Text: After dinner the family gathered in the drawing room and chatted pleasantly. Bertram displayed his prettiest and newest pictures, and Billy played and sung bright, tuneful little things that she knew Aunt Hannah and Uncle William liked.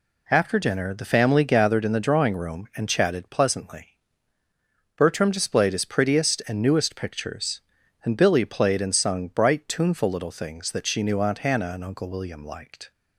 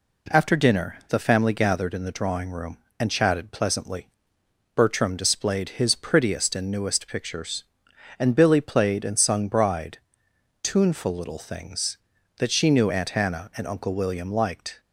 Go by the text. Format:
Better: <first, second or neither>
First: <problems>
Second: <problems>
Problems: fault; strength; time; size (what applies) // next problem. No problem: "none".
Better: first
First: none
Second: says "bride" for "bright"; at 9.4 s